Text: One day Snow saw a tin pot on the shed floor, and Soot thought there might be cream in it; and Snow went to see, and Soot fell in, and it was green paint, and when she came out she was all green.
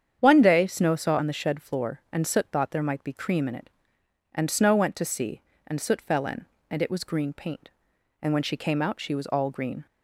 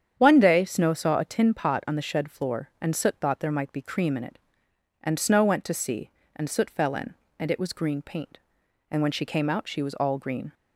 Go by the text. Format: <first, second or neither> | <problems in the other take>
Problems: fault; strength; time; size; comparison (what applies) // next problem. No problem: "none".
second | starts louder than the rest; strong; until 1.2 s; 8.5 dB; strong in the second // skips "a tin pot"; at 1.1 s